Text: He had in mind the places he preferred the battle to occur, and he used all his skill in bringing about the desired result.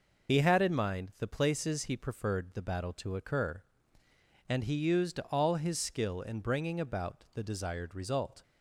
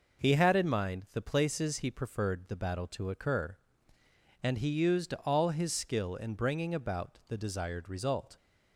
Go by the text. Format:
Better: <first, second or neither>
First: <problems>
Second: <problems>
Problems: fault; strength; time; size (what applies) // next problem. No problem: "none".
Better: second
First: loses the start of "He"; at 0.2 s; 35 ms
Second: none